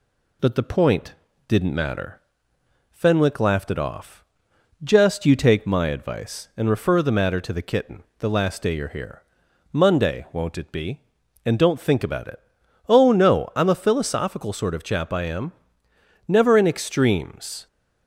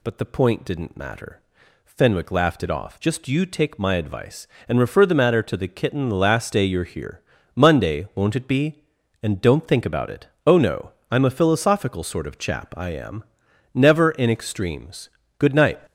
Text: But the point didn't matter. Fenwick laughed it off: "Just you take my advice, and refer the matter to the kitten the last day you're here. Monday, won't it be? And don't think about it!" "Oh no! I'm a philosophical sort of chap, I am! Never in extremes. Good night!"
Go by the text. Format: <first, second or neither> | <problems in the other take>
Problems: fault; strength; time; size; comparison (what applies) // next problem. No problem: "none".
second | pauses between "point" and "didn't"; slight; at 1.1 s; 0.34 s long // pauses between "kitten" and "the"; slight; at 8.0 s; 0.16 s long // stops before "Good night"; at 17.6 s